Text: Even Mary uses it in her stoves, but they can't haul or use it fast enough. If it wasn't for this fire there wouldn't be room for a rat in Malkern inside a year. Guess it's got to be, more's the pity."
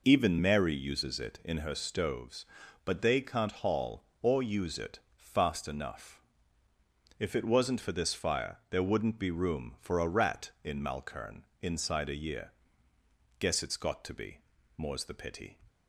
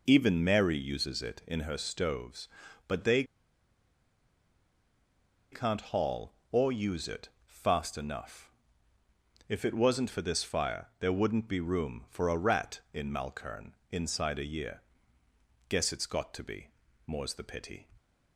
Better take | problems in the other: first | pauses between "they" and "can't"; strong; at 3.2 s; 2.2 s long // pauses between "it" and "fast"; slight; at 7.2 s; 0.18 s long; slight in the first // pauses between "Malkern" and "inside"; slight; at 13.7 s; 0.16 s long; slight in the first

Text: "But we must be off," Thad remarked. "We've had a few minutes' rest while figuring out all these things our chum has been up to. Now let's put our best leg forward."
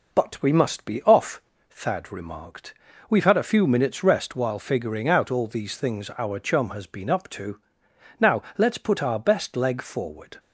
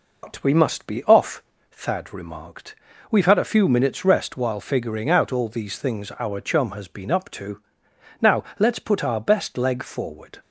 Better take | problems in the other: first | loses the start of "But"; at 0.2 s; 85 ms

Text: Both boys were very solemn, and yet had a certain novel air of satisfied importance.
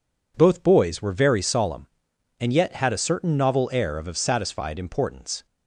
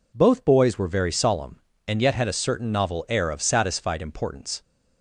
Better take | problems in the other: second | says "of" twice; at 4.0 s

